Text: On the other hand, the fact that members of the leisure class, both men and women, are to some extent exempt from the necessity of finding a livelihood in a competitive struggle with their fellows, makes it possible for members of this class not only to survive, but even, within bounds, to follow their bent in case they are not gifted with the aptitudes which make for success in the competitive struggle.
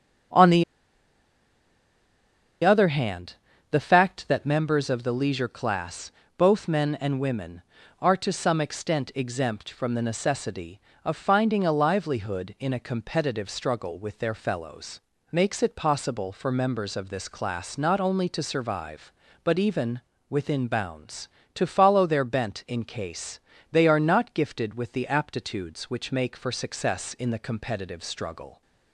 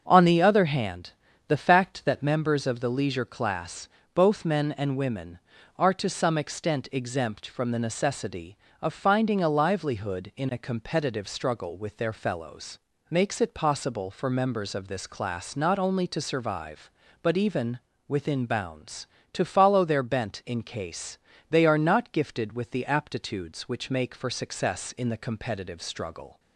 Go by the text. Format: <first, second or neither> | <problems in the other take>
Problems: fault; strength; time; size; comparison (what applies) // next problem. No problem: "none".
second | starts louder than the rest; until 3.3 s; 6.5 dB; also in the second // pauses between "the" and "other"; strong; at 0.6 s; 1.9 s long // pauses between "case" and "they"; slight; at 23.3 s; 0.32 s long; slight in the second